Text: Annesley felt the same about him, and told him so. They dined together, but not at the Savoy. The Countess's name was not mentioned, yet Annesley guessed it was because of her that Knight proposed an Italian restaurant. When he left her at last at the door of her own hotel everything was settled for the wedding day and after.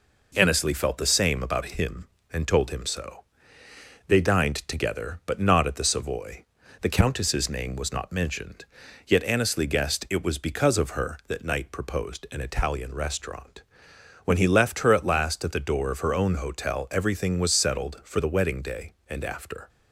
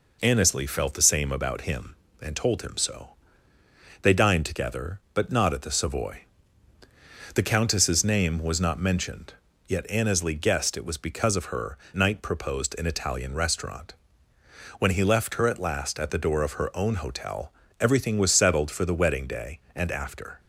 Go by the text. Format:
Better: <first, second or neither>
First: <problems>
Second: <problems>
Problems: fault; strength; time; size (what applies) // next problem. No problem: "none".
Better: first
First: none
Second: skips "that"; at 11.8 s // pauses between "hotel" and "everything"; slight; at 17.5 s; 0.26 s long